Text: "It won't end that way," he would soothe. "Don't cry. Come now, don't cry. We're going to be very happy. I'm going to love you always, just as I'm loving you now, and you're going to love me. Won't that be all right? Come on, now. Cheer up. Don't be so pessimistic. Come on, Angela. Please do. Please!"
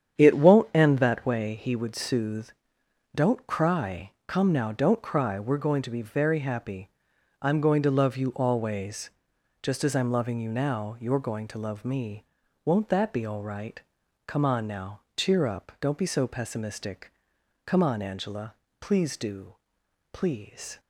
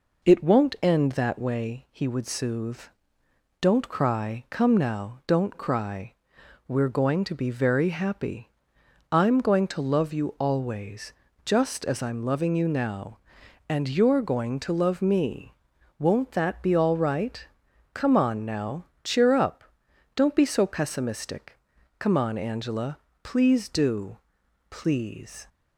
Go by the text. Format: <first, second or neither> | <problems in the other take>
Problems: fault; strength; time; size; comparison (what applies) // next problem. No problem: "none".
second | starts louder than the rest; strong; until 1.2 s; 8.5 dB // skips "and"; at 10.9 s